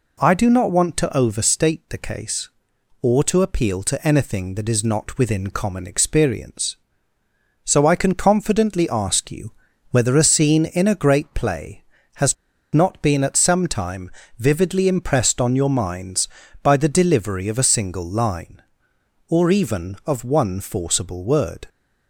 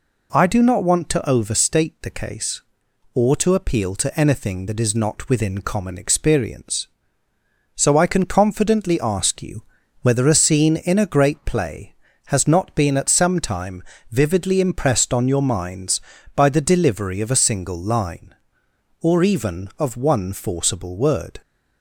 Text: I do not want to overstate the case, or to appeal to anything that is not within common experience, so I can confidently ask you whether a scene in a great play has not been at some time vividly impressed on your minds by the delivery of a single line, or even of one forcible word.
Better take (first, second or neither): second